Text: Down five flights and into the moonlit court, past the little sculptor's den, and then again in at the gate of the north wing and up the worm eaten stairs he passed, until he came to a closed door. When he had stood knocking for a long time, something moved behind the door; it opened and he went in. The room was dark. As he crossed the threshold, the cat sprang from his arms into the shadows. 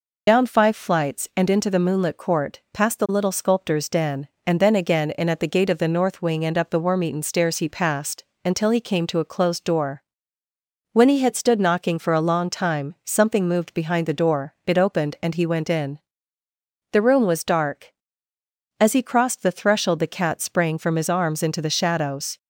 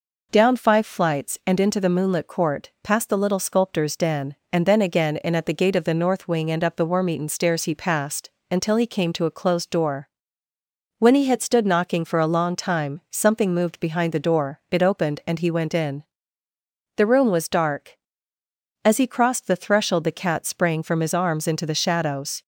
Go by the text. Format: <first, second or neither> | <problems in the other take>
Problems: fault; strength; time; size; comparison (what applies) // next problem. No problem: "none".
second | loses the start of "Down"; at 0.2 s; 65 ms